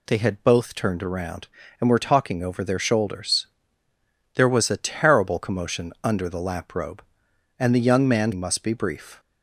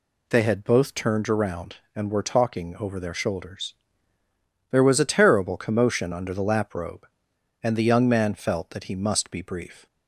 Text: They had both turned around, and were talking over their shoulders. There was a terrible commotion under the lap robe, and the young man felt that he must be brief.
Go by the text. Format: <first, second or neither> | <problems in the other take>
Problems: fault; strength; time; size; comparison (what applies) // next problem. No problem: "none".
second | skips "felt that he"; at 8.3 s